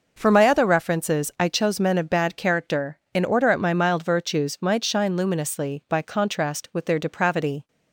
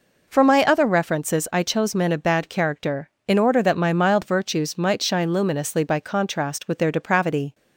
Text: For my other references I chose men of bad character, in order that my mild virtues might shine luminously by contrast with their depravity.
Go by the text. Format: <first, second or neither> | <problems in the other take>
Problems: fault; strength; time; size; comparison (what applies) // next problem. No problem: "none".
second | says "at" for "that"; at 3.4 s